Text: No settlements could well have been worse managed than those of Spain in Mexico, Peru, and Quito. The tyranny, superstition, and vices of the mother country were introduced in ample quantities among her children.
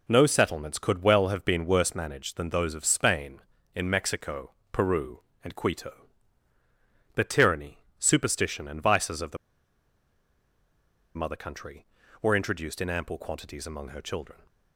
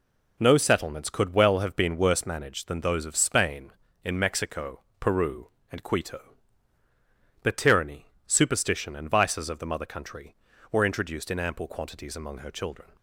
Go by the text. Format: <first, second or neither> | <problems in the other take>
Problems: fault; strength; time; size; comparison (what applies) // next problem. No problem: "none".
second | pauses between "the" and "mother"; strong; at 9.3 s; 1.7 s long